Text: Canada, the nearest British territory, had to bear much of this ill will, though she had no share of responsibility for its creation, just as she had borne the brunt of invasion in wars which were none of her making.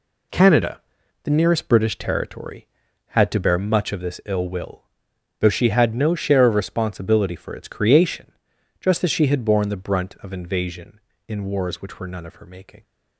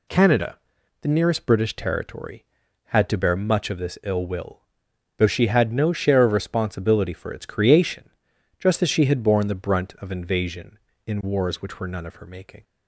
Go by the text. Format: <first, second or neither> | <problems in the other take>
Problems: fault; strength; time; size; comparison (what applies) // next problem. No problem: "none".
second | gets quieter; strong; throughout; 10 dB